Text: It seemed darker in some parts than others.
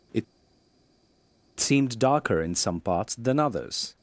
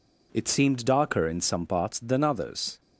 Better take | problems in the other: second | pauses between "It" and "seemed"; strong; at 0.2 s; 1.3 s long

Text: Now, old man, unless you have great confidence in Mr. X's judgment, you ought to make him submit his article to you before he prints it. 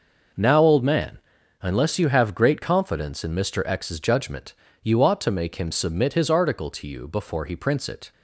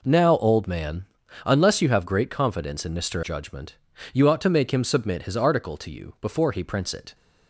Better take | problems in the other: first | skips "X's"; at 3.2 s

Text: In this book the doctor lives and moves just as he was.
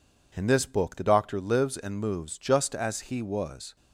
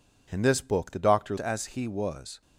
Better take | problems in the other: first | skips "lives and moves just"; at 1.3 s

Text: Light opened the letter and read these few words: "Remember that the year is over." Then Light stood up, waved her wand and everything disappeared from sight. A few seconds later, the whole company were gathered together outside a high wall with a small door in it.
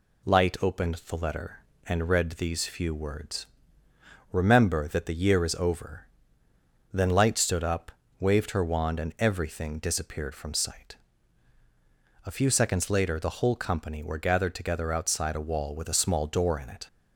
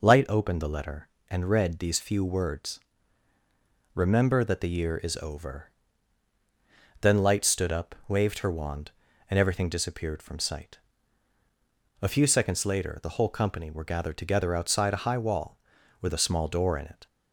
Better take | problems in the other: second | skips "high"; at 15.4 s

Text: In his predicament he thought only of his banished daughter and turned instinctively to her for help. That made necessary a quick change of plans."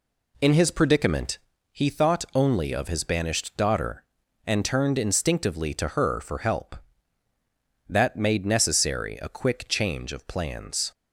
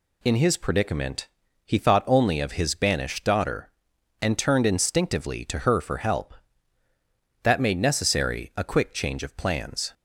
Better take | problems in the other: second | starts louder than the rest; slight; until 1.8 s; 2.5 dB // pauses between "predicament" and "he"; slight; at 1.3 s; 0.34 s long; also in the second

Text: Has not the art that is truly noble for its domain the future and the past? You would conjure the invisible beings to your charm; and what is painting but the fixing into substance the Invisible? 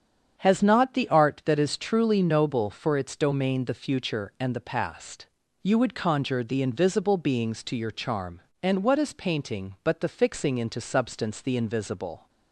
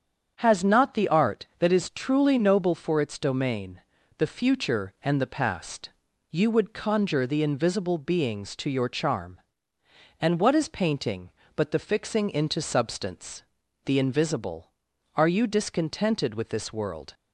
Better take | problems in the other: first | starts louder than the rest; strong; until 1.3 s; 7.5 dB; strong in the first // pauses between "domain" and "the"; slight; at 3.8 s; 0.36 s long // pauses between "substance" and "the"; at 13.4 s; 0.42 s long // goes on to say "Are you discontented with this world"; strong; from 15.1 s on; 2.0 s long

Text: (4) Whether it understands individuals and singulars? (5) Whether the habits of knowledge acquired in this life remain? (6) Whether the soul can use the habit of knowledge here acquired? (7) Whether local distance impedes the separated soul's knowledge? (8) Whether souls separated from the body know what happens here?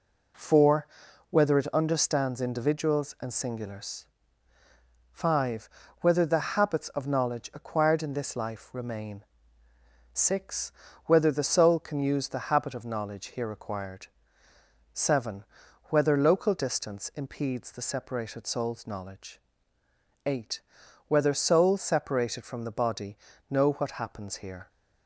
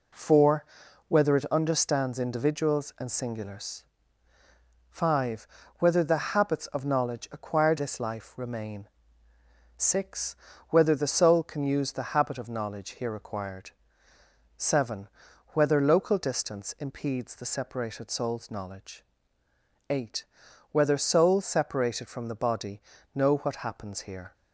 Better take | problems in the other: first | skips "in"; at 7.7 s // pauses between "body" and "know"; slight; at 22.7 s; 0.34 s long; slight in the first

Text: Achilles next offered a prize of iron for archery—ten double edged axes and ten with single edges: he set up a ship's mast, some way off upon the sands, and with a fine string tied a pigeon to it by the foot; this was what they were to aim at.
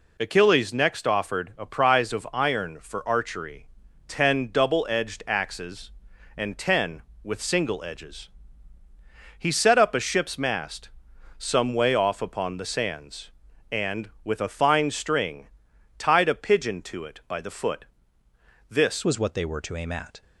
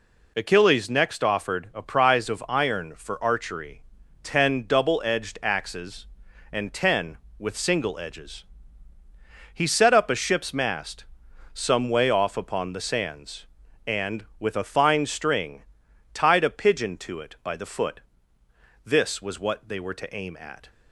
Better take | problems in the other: second | pauses between "string" and "tied"; noticeable; at 15.4 s; 0.50 s long; noticeable in the second // changes voice at "was"; from 19.0 s on; 1.2 s long

